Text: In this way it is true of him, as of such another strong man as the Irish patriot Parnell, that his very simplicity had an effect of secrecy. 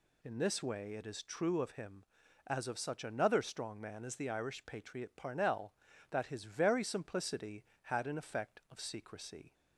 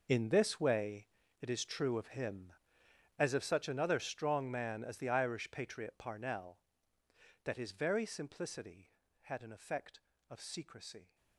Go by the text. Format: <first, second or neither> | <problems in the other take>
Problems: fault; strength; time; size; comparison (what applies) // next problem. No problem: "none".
first | gets quieter; strong; throughout; 15 dB // pauses between "way" and "it"; slight; at 1.0 s; 0.34 s long